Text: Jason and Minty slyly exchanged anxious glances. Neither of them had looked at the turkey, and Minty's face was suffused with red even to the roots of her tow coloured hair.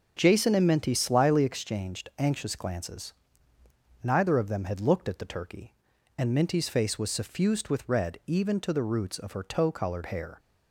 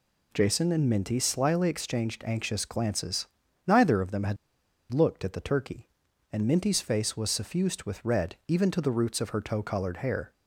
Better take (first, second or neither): first